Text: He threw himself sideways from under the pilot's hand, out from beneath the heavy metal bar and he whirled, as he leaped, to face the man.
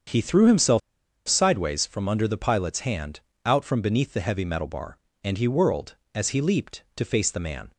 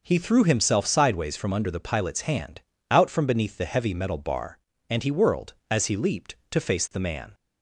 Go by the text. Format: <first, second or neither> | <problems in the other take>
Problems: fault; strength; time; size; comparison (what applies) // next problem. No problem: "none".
second | starts louder than the rest; strong; until 1.5 s; 7.5 dB // pauses between "himself" and "sideways"; noticeable; at 0.7 s; 0.48 s long